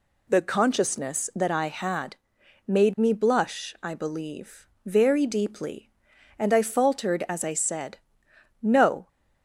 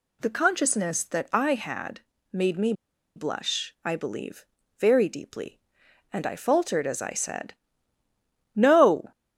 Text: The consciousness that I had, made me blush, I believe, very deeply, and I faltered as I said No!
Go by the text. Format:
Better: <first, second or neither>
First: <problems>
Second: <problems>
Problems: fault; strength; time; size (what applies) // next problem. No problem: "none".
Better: first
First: pauses between "said" and "No"; noticeable; at 7.9 s; 0.64 s long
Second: pauses between "me" and "blush"; at 2.7 s; 0.43 s long // pauses between "said" and "No"; at 7.5 s; 1.0 s long